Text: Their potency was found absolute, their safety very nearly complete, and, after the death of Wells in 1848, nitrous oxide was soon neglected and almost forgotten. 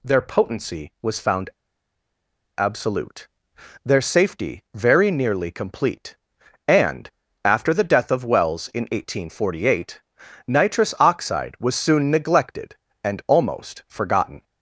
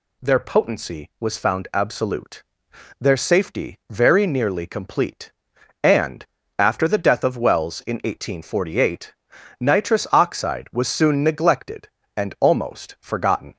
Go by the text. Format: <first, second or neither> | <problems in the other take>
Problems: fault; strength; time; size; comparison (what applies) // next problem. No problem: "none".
second | pauses between "found" and "absolute"; at 1.5 s; 1.0 s long